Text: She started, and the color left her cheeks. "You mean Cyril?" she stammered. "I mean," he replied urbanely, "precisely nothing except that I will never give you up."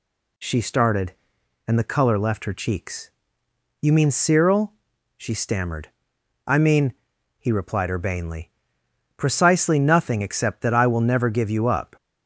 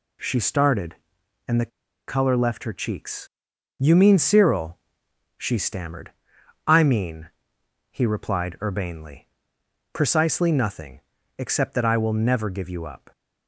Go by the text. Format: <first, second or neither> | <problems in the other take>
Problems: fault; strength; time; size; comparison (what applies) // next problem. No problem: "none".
first | pauses between "the" and "color"; at 1.7 s; 0.39 s long // pauses between "nothing" and "except"; slight; at 11.0 s; 0.36 s long